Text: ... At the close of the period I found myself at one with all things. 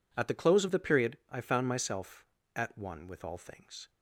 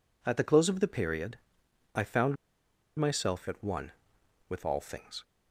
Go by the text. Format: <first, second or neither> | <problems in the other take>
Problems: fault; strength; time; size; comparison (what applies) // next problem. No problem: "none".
first | pauses between "period" and "I"; noticeable; at 1.3 s; 0.60 s long // pauses between "found" and "myself"; noticeable; at 2.3 s; 0.61 s long